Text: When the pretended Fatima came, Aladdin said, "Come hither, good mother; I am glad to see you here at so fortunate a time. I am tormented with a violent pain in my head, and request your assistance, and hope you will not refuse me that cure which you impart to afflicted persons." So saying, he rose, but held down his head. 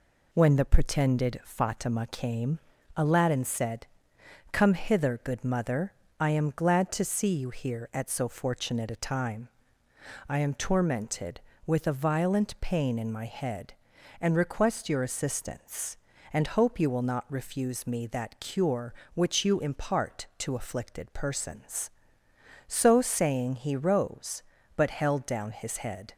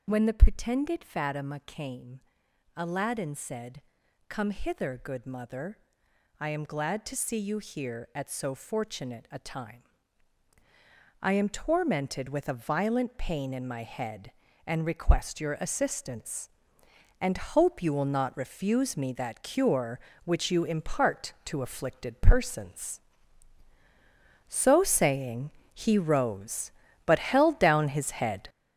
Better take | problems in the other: first | gets louder; throughout; 7 dB

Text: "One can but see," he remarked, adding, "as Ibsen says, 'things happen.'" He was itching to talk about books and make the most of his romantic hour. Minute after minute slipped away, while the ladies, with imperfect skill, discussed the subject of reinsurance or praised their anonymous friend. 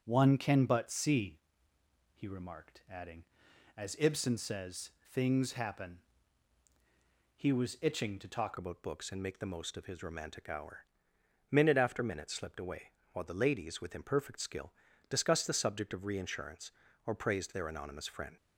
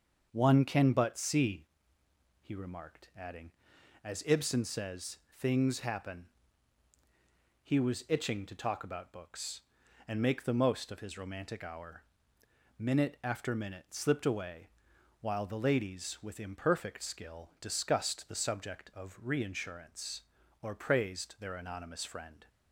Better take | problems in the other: second | starts louder than the rest; until 1.0 s; 6 dB; also in the second // changes voice at "about"; from 8.5 s on; 9.8 s long

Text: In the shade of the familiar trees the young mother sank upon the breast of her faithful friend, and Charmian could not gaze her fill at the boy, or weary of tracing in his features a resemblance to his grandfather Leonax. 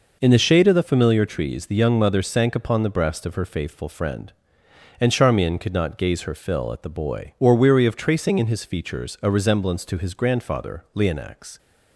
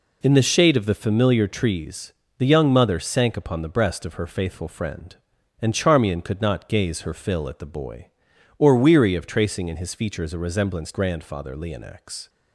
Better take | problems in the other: first | pauses between "trees" and "the"; slight; at 2.1 s; 0.26 s long // skips "to his"; at 10.9 s

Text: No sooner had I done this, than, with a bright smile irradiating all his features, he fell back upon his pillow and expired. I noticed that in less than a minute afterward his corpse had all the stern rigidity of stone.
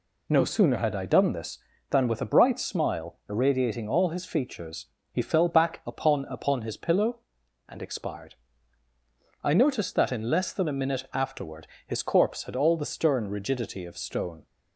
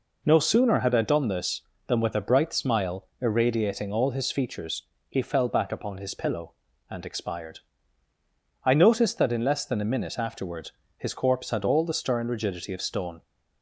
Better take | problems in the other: second | says "upon" twice; at 6.2 s // pauses between "afterward" and "his"; slight; at 11.6 s; 0.20 s long; slight in the second

